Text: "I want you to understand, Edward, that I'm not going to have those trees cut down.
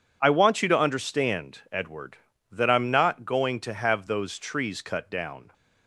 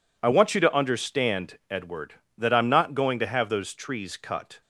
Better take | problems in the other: first | stops before "down"; at 4.6 s

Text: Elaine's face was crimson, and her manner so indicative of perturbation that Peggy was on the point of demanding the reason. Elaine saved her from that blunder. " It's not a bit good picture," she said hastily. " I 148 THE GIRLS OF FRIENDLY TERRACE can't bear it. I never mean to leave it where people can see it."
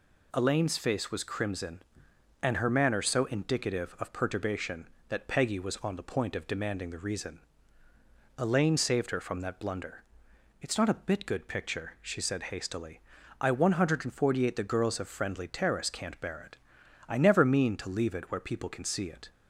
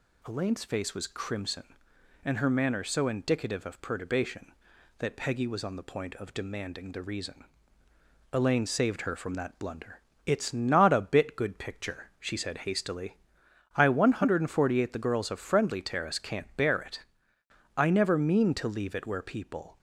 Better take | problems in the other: first | stops before "can see it"; at 19.7 s

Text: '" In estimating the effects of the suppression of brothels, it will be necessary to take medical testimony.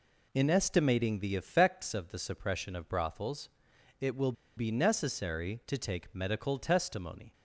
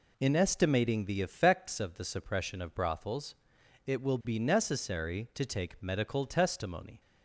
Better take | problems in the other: second | pauses between "will" and "be"; slight; at 4.3 s; 0.24 s long

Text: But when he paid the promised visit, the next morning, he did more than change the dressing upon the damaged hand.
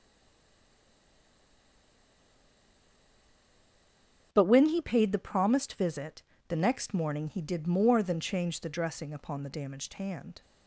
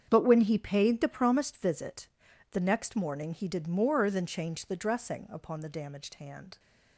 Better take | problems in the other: second | stays silent before the first word; strong; until 4.3 s; 4.3 s long // starts louder than the rest; until 5.3 s; 7 dB; strong in the second

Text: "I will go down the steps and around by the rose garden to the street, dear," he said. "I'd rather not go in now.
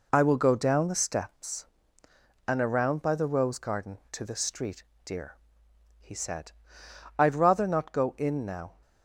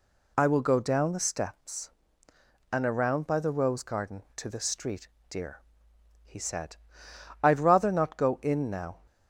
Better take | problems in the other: second | gets quieter; noticeable; throughout; 5 dB

